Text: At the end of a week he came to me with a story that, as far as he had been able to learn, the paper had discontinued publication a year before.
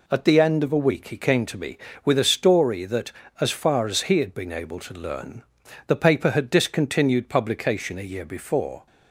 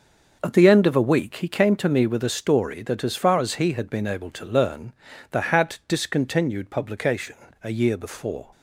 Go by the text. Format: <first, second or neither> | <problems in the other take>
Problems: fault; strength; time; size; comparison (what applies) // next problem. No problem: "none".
first | skips "paper"; at 5.4 s // pauses between "publication" and "a"; slight; at 7.3 s; 0.30 s long